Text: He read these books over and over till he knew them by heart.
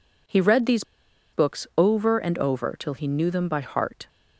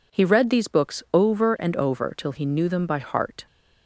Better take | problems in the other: second | pauses between "these" and "books"; noticeable; at 0.8 s; 0.50 s long

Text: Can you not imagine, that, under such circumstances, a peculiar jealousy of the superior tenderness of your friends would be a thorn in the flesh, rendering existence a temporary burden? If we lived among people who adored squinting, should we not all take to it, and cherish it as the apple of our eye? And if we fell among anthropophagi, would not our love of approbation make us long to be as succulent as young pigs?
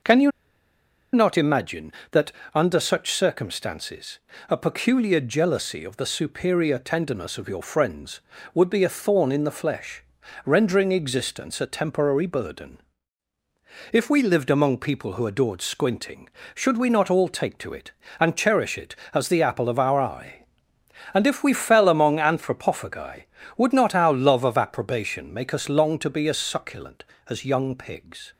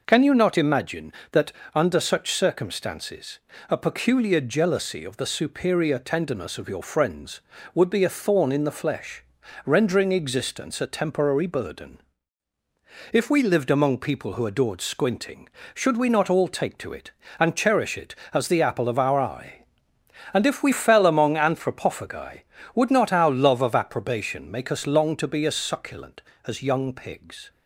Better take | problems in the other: second | pauses between "you" and "not"; noticeable; at 0.3 s; 0.83 s long

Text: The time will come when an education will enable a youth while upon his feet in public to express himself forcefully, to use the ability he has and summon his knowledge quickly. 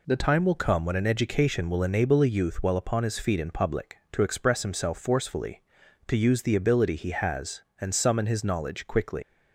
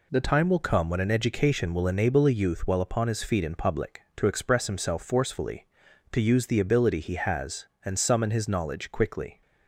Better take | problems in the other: second | leaves "quickly" unfinished; at 9.2 s; 140 ms

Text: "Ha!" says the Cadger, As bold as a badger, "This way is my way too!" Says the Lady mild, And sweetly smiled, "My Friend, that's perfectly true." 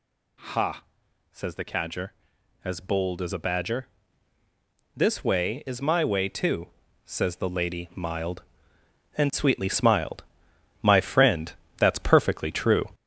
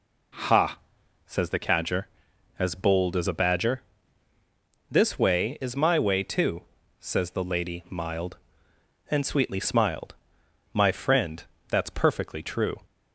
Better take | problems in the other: second | gets louder; noticeable; throughout; 5.5 dB

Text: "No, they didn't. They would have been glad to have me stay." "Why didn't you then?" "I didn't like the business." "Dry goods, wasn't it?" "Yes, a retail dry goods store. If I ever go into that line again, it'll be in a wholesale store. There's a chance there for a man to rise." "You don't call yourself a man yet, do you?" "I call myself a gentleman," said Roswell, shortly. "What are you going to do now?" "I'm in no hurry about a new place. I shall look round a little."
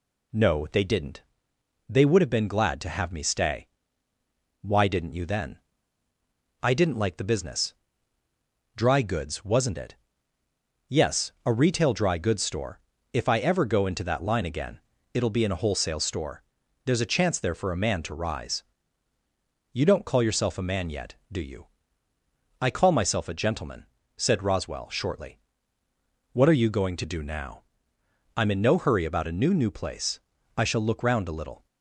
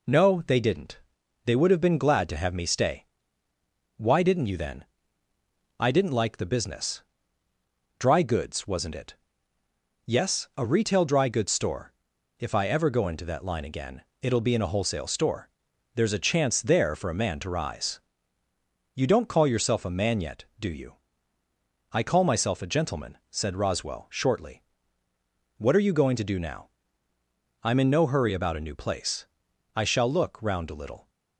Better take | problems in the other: second | says "new" twice; at 29.5 s

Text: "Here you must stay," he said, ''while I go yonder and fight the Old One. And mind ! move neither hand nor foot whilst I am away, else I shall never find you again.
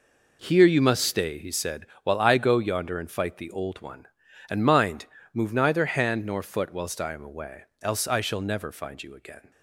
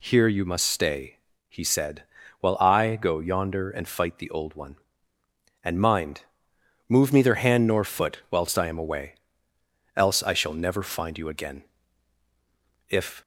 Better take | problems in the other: first | goes on to say "If"; slight; from 12.8 s on; 0.32 s long

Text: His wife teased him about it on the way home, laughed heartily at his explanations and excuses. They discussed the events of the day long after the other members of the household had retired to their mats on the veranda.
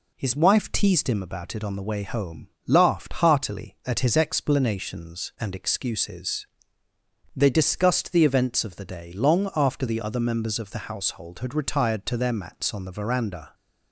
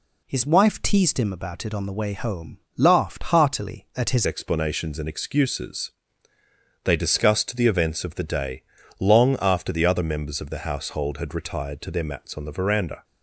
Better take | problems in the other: first | changes voice at "explanations"; from 4.2 s on; 8.8 s long // pauses between "day" and "long"; at 8.6 s; 0.38 s long

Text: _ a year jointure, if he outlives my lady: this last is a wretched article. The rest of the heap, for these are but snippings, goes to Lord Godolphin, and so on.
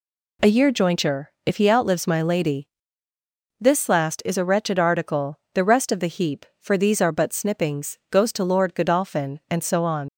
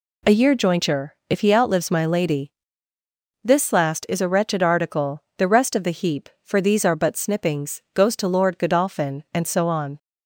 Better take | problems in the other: second | leaves "on" unfinished; at 10.0 s; 55 ms

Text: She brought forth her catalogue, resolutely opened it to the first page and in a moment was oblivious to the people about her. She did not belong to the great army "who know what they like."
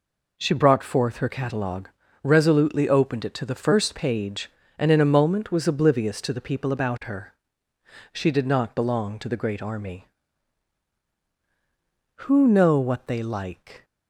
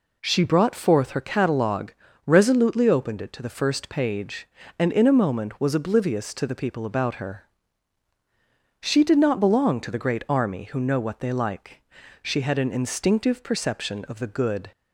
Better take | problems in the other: first | goes on to say "She had an instinctive perception of the good"; strong; from 12.2 s on; 2.4 s long

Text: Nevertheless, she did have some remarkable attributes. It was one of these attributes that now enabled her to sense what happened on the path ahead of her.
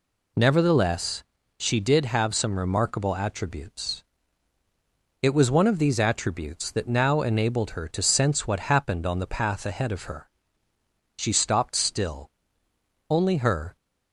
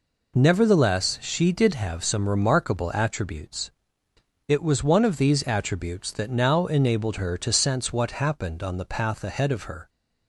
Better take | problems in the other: second | goes on to say "She stopped still only her"; strong; from 11.1 s on; 2.6 s long

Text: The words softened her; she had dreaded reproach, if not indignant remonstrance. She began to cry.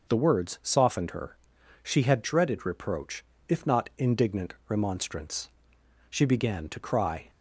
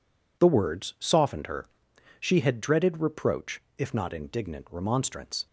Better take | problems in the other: first | stops before "She began to cry"; at 5.4 s

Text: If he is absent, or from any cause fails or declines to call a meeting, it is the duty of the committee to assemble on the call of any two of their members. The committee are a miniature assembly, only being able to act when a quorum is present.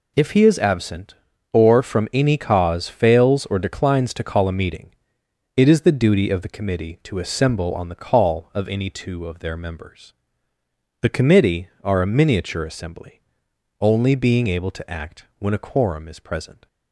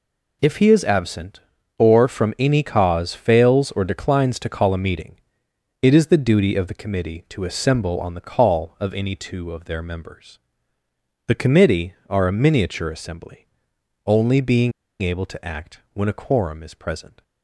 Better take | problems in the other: first | pauses between "being" and "able"; slight; at 14.7 s; 0.28 s long

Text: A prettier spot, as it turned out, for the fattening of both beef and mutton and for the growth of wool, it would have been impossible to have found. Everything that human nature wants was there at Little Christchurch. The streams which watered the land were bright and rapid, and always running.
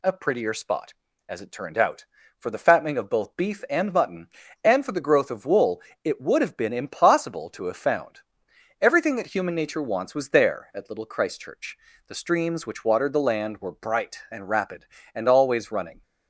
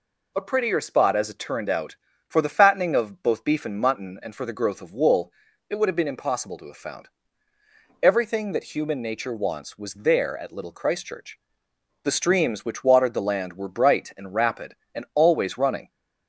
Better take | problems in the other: neither | none

